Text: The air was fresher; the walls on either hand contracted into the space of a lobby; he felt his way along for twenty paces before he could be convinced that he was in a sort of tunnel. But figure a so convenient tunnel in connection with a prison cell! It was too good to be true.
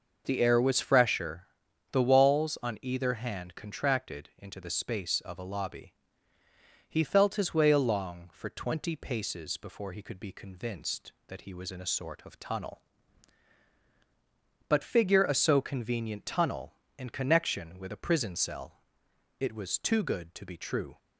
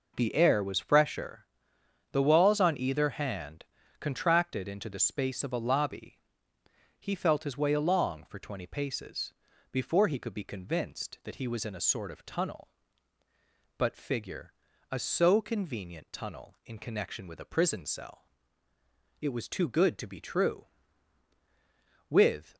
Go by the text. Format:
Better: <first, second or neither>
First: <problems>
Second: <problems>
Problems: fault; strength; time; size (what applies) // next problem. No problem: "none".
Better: first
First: none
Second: pauses between "hand" and "contracted"; slight; at 3.6 s; 0.36 s long // pauses between "paces" and "before"; at 9.3 s; 0.38 s long // pauses between "figure" and "a"; at 14.5 s; 0.40 s long // goes on to say "With"; slight; from 22.0 s on; 0.48 s long